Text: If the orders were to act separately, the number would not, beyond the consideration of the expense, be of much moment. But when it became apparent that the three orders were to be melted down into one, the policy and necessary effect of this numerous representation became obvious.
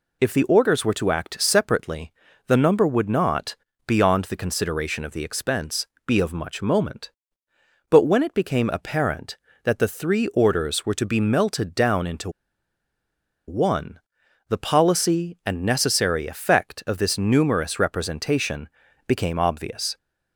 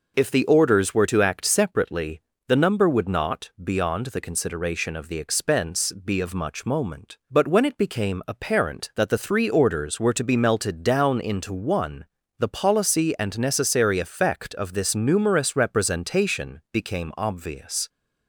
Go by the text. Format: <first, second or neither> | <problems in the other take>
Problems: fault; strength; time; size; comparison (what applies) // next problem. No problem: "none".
second | pauses between "into" and "one"; at 12.2 s; 1.1 s long // pauses between "representation" and "became"; at 18.6 s; 0.40 s long